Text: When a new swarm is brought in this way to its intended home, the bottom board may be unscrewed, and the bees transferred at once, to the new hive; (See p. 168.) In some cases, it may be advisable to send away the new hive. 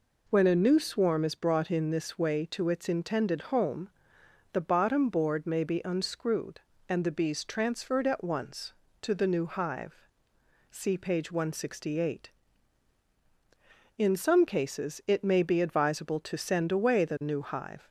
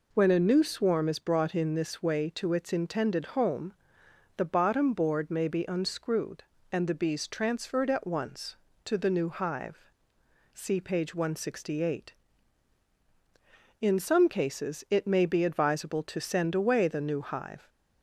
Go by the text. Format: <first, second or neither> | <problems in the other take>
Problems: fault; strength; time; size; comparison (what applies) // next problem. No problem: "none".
neither | none